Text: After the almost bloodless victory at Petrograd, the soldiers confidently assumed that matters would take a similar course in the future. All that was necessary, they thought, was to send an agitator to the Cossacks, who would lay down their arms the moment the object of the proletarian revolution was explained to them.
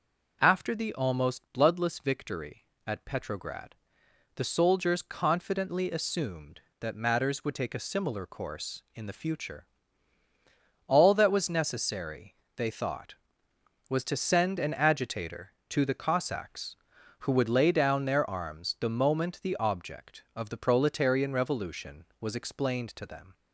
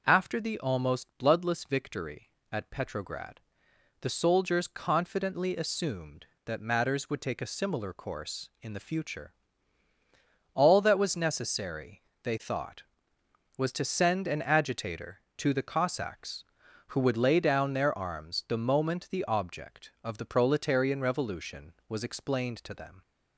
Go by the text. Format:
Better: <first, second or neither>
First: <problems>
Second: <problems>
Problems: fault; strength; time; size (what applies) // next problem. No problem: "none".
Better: neither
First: none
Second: none